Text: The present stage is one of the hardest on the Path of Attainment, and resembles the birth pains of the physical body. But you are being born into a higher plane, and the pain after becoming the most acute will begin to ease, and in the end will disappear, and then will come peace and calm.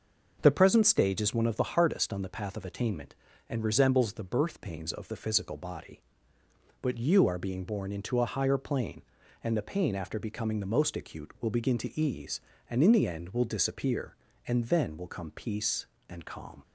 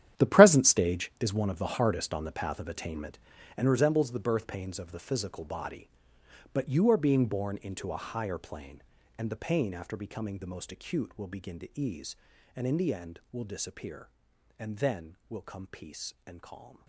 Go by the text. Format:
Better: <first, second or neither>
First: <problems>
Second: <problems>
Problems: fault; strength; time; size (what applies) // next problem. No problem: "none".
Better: first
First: none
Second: gets quieter; strong; throughout; 14 dB